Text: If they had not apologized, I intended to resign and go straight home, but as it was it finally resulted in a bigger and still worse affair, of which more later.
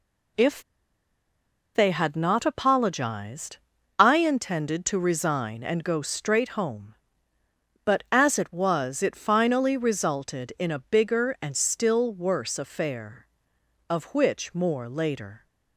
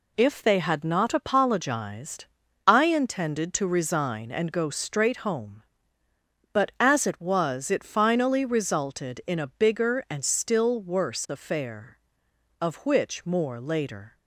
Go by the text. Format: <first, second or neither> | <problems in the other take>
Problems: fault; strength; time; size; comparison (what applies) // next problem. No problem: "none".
second | pauses between "If" and "they"; at 0.6 s; 1.1 s long